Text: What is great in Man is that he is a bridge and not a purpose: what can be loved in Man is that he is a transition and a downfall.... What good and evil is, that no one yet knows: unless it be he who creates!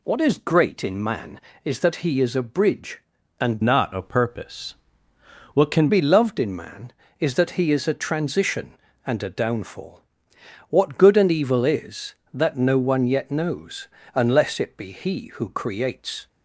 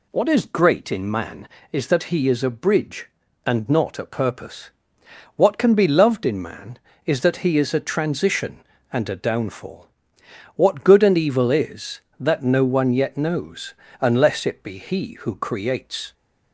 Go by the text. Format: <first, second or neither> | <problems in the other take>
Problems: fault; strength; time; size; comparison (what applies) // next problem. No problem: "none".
second | changes voice from "not" to "can"; from 3.6 to 5.8 s; 2.2 s long